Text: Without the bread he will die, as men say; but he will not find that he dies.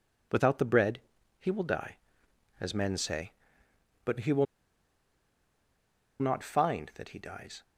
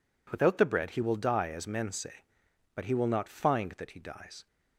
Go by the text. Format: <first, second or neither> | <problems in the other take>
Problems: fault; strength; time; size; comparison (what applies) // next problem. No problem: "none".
second | pauses between "bread" and "he"; at 0.9 s; 0.42 s long // pauses between "will" and "not"; strong; at 4.4 s; 1.7 s long